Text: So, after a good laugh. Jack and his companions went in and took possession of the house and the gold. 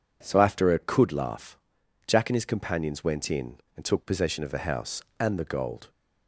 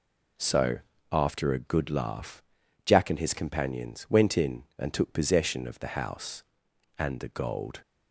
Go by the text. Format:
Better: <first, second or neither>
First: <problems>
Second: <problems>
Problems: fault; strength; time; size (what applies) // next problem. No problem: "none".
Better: second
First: says "could" for "good"; at 0.7 s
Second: none